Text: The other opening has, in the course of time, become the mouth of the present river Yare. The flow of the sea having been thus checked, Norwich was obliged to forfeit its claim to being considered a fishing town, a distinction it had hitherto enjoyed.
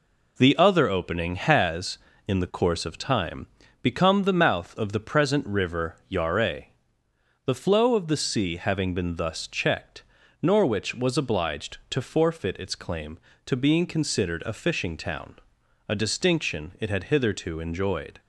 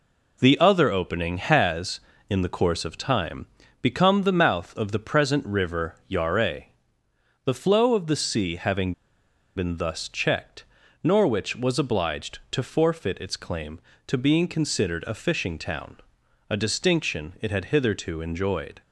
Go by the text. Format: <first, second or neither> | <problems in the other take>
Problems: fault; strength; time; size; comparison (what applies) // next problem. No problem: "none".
first | pauses between "having" and "been"; noticeable; at 8.9 s; 0.62 s long